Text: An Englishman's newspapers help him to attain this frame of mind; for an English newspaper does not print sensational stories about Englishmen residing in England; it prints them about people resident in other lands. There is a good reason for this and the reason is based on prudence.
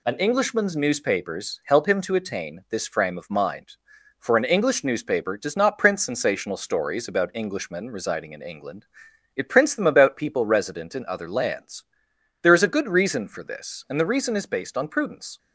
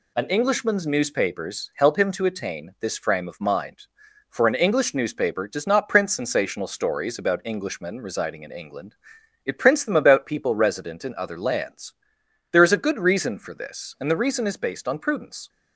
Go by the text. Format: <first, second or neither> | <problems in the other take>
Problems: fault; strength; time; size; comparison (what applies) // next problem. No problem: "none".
neither | none